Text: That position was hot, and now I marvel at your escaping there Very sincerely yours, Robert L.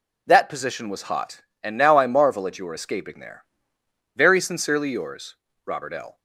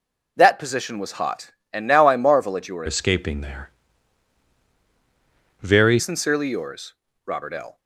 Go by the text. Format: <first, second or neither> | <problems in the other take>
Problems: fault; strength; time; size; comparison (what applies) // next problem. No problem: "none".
first | changes voice from "escaping" to "Very"; from 2.8 to 5.9 s; 3.1 s long // pauses between "there" and "Very"; strong; at 3.7 s; 1.9 s long; noticeable in the first